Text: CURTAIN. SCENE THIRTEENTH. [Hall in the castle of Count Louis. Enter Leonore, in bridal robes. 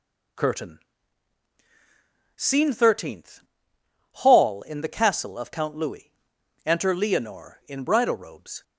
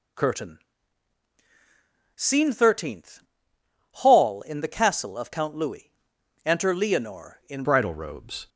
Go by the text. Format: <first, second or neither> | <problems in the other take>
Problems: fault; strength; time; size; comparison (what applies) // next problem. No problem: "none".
first | changes voice at "bridal"; from 7.6 s on; 0.8 s long